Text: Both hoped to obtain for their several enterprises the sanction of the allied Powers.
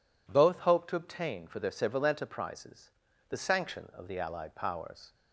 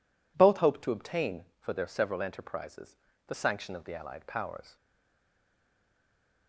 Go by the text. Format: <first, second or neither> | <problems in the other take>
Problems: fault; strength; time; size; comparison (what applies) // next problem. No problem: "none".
first | pauses between "enterprises" and "the"; slight; at 2.9 s; 0.30 s long; also in the first // stays silent after the last word; noticeable; from 4.7 s on; 1.7 s long